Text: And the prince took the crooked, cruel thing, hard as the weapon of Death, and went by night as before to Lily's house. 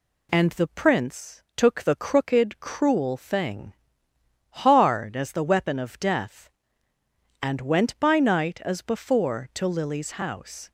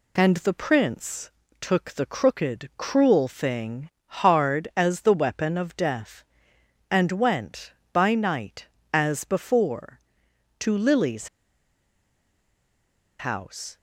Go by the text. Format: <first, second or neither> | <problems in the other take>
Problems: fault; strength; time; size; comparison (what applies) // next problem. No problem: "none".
first | pauses between "prince" and "took"; slight; at 1.3 s; 0.30 s long // pauses between "Lily's" and "house"; strong; at 11.2 s; 1.9 s long